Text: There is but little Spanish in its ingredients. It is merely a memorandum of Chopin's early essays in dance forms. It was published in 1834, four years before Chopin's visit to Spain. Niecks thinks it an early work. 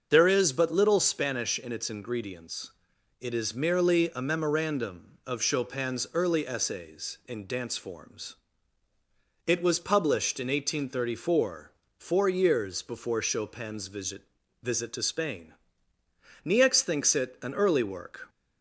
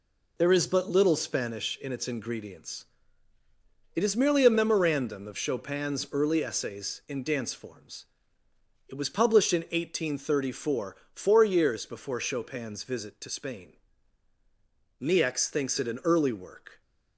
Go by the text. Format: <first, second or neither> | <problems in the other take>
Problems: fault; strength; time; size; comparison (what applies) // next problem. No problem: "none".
second | starts louder than the rest; until 1.1 s; 6.5 dB // says "visit" twice; at 14.6 s